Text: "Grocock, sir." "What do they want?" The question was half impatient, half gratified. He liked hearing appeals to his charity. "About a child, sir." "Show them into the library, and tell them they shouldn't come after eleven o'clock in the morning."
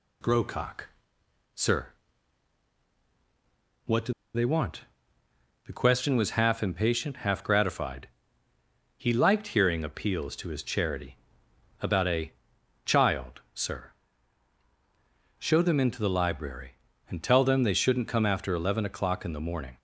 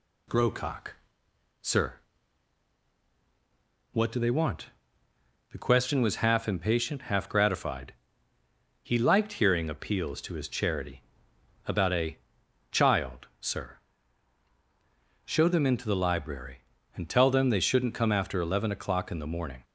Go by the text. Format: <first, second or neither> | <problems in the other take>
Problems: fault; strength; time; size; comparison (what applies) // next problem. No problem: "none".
second | pauses between "do" and "they"; slight; at 4.1 s; 0.22 s long // pauses between "a" and "child"; noticeable; at 12.3 s; 0.50 s long; noticeable in the second